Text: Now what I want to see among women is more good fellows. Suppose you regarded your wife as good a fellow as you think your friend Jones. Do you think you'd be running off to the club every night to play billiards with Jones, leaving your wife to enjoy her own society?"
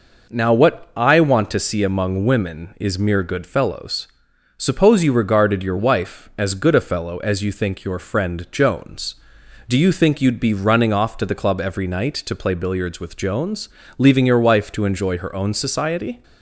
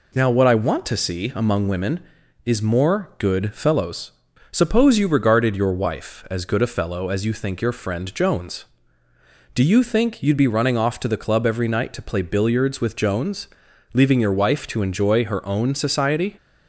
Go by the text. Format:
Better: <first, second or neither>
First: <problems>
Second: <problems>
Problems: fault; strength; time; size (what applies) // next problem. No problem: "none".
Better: second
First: says "mere" for "more"; at 2.9 s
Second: none